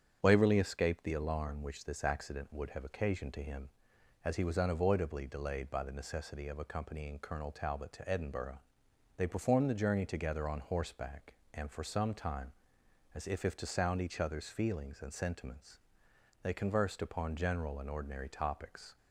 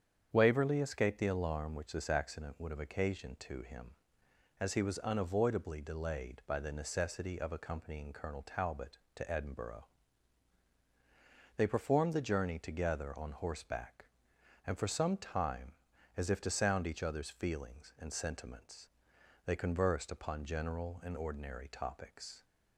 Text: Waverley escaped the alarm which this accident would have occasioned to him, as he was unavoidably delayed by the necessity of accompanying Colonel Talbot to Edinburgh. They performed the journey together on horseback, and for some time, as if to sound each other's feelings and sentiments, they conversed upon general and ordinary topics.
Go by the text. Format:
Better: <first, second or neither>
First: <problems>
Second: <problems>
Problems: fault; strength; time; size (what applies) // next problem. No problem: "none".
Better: second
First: starts louder than the rest; strong; until 1.2 s; 8 dB // says "if" twice; at 13.4 s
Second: starts louder than the rest; strong; until 1.3 s; 8 dB